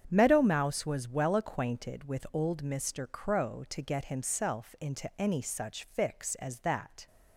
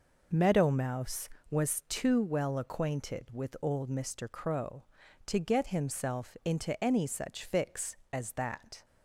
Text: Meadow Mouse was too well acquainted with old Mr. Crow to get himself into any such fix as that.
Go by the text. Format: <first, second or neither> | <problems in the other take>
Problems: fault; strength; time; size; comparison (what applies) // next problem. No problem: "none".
second | starts louder than the rest; strong; until 1.1 s; 8 dB // skips "too"; at 1.0 s